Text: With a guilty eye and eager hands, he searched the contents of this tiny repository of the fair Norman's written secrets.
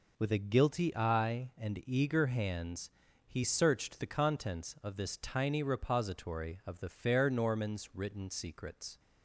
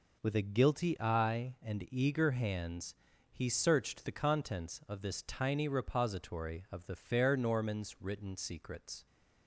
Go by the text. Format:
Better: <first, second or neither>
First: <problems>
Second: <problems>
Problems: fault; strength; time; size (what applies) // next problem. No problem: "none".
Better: neither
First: none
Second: none